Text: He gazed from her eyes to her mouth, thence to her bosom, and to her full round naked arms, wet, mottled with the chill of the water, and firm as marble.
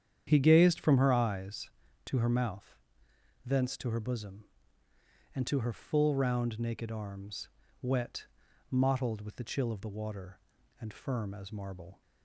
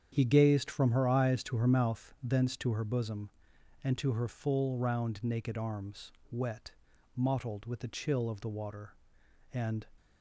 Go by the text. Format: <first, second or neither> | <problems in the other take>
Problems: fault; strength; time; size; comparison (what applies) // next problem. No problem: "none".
first | starts louder than the rest; strong; until 1.1 s; 8.5 dB; strong in the first // stops before "firm as marble"; at 9.9 s